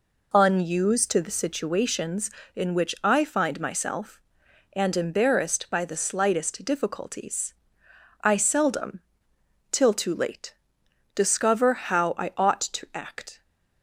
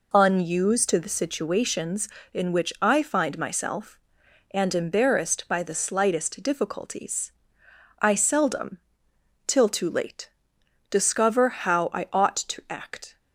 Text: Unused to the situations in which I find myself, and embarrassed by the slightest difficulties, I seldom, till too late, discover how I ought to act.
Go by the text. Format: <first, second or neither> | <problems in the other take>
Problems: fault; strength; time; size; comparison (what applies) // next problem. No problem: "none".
neither | none